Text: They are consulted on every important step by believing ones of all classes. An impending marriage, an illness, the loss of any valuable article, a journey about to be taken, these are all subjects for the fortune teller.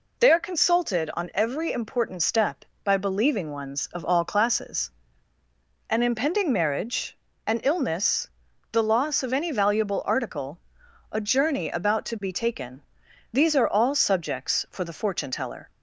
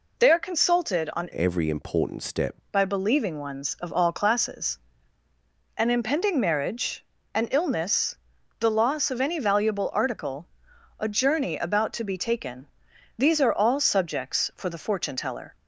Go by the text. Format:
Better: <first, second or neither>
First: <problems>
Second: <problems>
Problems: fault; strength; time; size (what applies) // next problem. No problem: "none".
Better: first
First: none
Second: changes voice from "every" to "step"; from 1.3 to 2.5 s; 1.2 s long